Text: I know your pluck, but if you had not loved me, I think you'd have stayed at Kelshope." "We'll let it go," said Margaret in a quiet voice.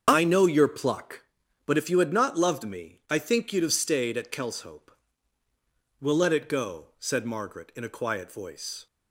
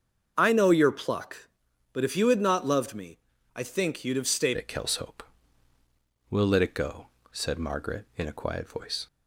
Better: first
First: starts louder than the rest; until 1.0 s; 7 dB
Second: starts louder than the rest; until 1.3 s; 6.5 dB // changes voice at "at"; from 4.5 s on; 4.5 s long

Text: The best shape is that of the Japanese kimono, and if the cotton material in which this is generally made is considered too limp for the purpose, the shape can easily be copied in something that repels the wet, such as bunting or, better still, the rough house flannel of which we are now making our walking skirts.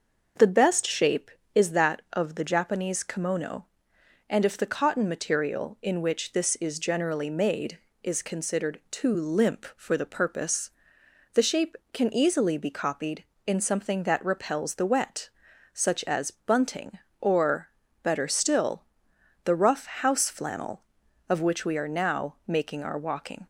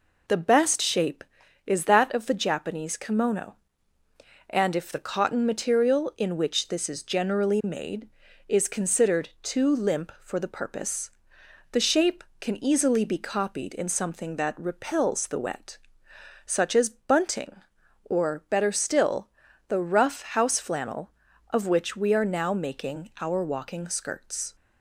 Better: second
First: starts louder than the rest; until 1.6 s; 6.5 dB // stops before "skirts"; at 23.4 s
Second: none

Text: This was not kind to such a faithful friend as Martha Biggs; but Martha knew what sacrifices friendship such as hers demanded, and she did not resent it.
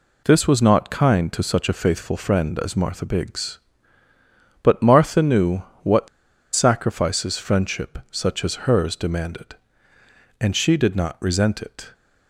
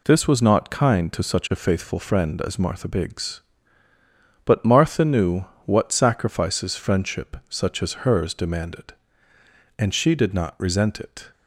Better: second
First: pauses between "knew" and "what"; slight; at 5.6 s; 0.18 s long // pauses between "what" and "sacrifices"; noticeable; at 6.0 s; 0.47 s long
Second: pauses between "knew" and "what"; slight; at 5.4 s; 0.18 s long

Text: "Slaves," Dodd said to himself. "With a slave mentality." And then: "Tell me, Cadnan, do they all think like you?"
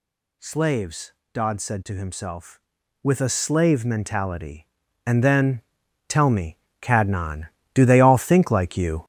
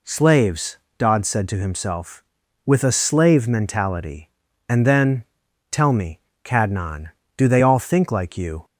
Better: second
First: gets louder; throughout; 7 dB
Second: none

